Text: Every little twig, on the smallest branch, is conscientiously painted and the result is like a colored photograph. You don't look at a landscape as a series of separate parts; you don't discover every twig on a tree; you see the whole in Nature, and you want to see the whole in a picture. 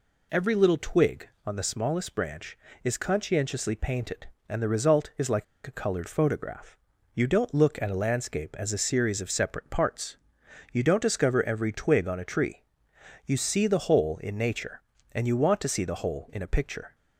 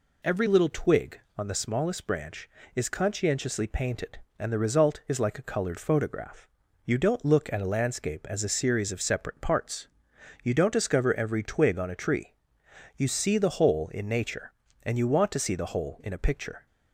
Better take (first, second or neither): second